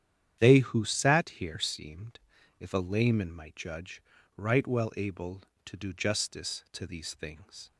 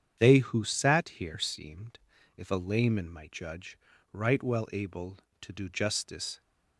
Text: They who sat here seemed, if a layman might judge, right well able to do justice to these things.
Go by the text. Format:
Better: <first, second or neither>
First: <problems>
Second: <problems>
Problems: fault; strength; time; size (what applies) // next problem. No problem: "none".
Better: first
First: starts louder than the rest; strong; until 1.4 s; 9.5 dB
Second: starts louder than the rest; strong; until 1.2 s; 8 dB // stops before "to these things"; at 6.4 s